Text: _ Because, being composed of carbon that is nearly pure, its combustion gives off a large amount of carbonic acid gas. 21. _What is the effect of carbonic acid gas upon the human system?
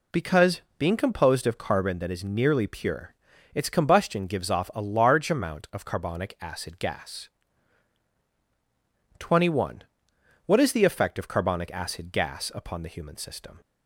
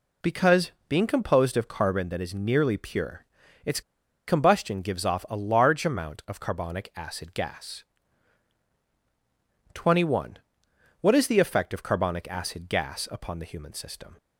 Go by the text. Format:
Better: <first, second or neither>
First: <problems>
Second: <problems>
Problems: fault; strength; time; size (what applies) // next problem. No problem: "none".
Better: first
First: none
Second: pauses between "its" and "combustion"; noticeable; at 3.8 s; 0.46 s long